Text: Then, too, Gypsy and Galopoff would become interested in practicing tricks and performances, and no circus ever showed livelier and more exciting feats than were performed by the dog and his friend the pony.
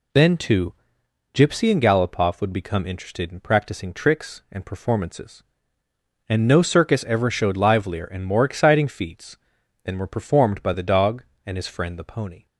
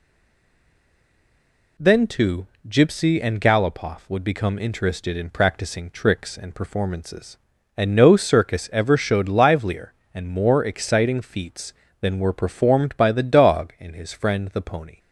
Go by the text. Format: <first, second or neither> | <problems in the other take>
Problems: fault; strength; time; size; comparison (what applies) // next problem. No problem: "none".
first | stays silent before the first word; noticeable; until 1.7 s; 1.7 s long